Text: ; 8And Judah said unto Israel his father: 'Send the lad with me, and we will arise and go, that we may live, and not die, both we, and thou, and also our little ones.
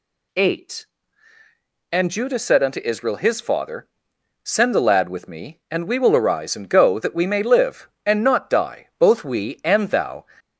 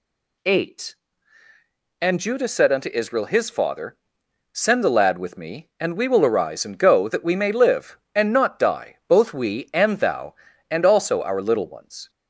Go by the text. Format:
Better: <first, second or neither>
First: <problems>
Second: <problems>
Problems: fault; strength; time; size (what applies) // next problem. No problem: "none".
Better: second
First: stops before "and also our little ones"; at 10.3 s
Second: none